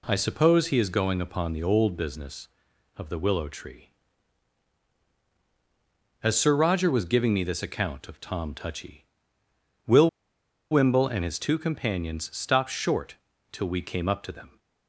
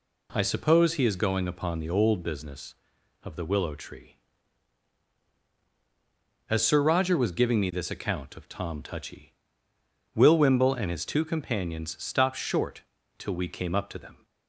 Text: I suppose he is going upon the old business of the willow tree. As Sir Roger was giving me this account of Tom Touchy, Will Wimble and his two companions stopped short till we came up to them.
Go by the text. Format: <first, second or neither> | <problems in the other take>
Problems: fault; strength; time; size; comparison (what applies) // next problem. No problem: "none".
second | pauses between "Will" and "Wimble"; noticeable; at 10.0 s; 0.62 s long // pauses between "short" and "till"; at 13.1 s; 0.38 s long; also in the second